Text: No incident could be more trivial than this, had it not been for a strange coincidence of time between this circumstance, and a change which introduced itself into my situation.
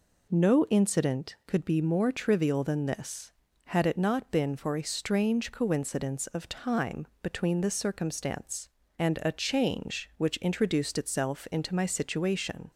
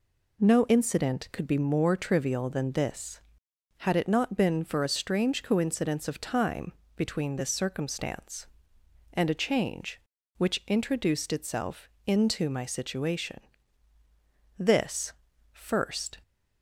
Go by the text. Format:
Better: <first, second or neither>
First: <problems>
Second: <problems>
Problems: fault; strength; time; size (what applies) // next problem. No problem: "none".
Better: first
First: none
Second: pauses between "time" and "between"; slight; at 6.7 s; 0.22 s long // pauses between "itself" and "into"; slight; at 11.8 s; 0.16 s long // goes on to say "This first"; from 14.5 s on; 1.6 s long